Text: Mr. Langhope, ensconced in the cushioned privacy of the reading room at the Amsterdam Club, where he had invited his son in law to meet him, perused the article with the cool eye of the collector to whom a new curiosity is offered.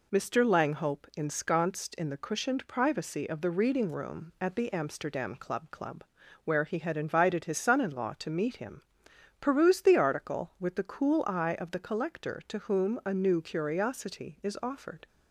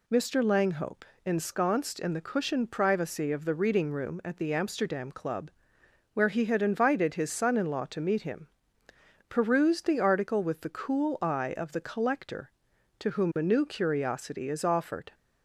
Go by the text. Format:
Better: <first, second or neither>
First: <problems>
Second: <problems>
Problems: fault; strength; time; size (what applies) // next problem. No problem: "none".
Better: second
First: says "Club" twice; at 5.7 s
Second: none